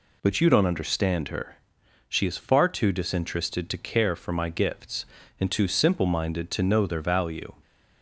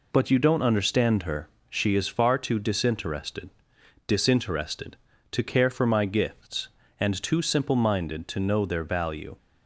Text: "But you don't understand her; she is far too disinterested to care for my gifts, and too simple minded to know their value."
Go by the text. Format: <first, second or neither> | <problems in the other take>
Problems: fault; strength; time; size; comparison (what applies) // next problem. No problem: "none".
first | says "disinterested" twice; at 4.0 s